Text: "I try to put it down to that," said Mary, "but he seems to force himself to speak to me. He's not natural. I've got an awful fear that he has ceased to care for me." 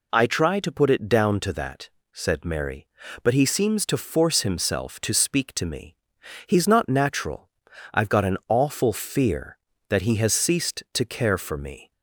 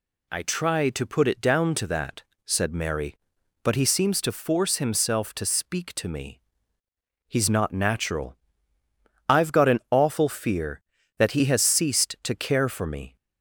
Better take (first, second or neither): neither